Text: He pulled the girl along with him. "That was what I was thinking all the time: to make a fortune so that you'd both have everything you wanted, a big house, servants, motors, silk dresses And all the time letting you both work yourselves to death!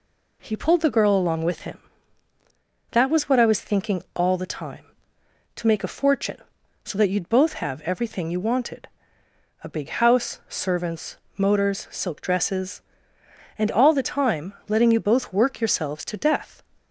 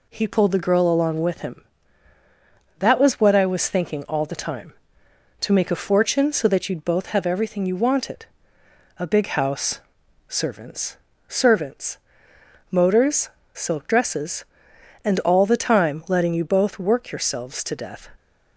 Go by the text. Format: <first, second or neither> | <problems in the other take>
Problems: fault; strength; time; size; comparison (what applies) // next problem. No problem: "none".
first | says "servants" twice; at 11.2 s